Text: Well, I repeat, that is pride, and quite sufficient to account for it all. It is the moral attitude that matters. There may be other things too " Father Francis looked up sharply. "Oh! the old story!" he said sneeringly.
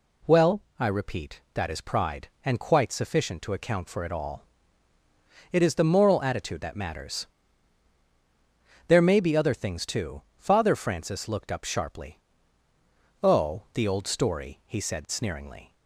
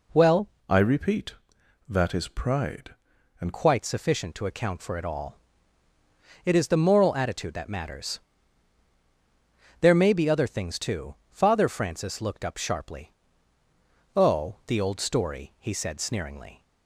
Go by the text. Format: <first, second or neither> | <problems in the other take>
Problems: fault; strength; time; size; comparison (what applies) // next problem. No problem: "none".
first | changes voice from "I" to "and"; from 0.6 to 3.5 s; 2.9 s long